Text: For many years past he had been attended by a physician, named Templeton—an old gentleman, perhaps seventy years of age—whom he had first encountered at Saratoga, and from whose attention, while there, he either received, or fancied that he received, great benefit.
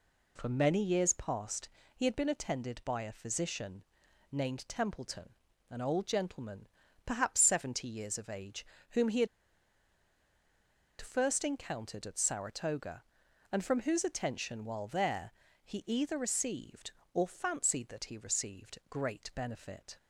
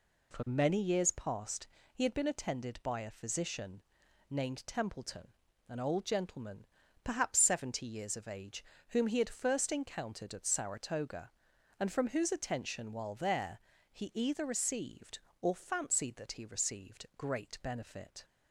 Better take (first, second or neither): second